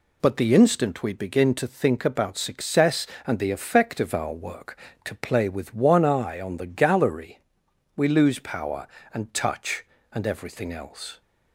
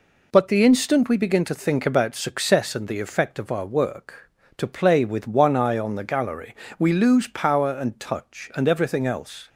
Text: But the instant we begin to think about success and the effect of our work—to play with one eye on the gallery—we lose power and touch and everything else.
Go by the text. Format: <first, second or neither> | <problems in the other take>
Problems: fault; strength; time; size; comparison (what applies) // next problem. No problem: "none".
neither | none